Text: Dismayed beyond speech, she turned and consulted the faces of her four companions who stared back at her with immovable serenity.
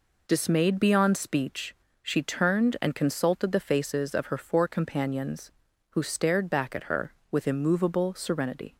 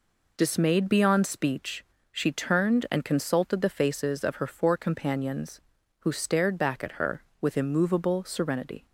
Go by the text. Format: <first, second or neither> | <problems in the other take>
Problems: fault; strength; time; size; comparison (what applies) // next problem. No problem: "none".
neither | none